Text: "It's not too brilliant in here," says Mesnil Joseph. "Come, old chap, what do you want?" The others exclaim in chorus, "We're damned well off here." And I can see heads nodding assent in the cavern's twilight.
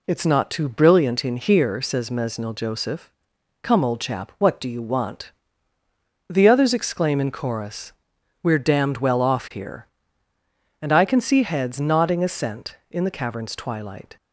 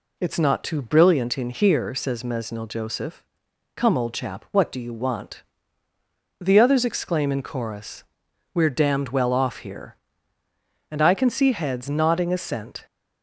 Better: first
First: none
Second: stops before "in the cavern's twilight"; at 12.8 s

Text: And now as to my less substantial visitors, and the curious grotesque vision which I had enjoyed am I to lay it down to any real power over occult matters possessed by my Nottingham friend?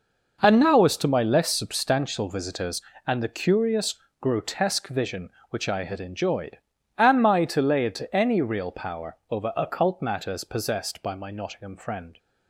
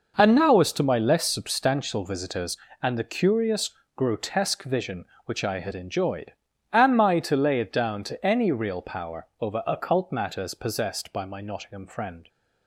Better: second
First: pauses between "curious" and "grotesque"; slight; at 3.9 s; 0.26 s long // pauses between "enjoyed" and "am"; at 6.5 s; 0.38 s long // skips "down"; at 7.9 s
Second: pauses between "curious" and "grotesque"; slight; at 3.7 s; 0.26 s long // pauses between "enjoyed" and "am"; at 6.3 s; 0.38 s long

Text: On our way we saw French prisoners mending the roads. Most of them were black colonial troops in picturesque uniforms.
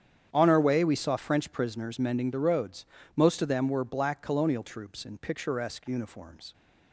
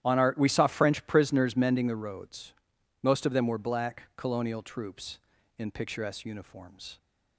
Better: first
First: starts louder than the rest; strong; until 1.3 s; 9 dB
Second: starts louder than the rest; strong; until 1.0 s; 11.5 dB // skips "way"; at 0.3 s

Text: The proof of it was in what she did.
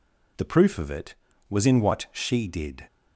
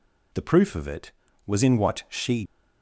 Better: first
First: none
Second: stops before "did"; at 2.4 s

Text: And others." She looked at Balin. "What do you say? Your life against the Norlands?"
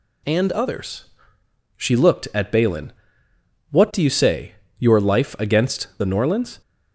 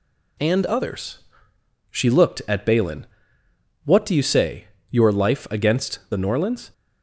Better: first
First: none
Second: gets quieter; slight; throughout; 2 dB

